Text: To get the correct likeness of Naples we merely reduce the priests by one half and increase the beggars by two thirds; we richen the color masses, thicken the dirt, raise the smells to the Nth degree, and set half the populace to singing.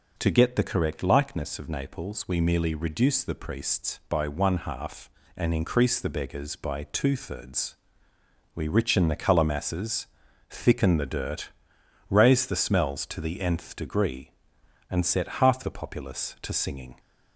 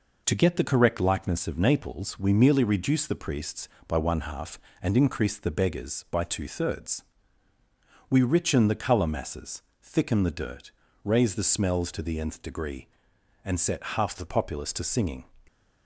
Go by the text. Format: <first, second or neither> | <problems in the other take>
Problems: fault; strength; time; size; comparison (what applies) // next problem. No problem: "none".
neither | none